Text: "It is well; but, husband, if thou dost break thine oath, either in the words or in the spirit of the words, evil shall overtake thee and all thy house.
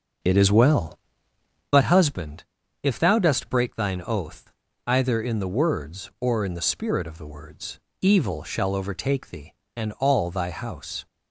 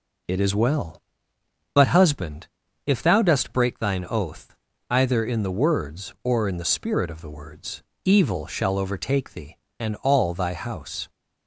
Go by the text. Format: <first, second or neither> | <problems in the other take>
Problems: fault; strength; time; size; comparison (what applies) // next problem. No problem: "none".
second | starts louder than the rest; noticeable; until 1.7 s; 6 dB